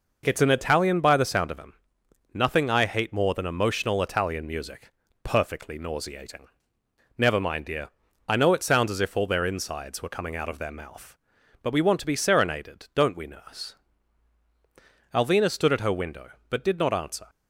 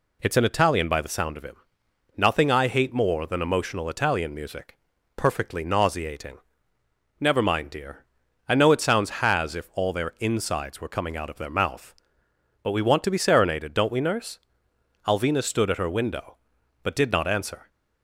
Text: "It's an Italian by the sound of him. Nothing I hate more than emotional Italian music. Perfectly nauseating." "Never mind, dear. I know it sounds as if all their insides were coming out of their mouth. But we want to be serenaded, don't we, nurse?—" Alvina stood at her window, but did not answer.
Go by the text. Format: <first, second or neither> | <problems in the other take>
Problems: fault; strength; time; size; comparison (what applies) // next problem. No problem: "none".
first | says "has" for "as"; at 9.2 s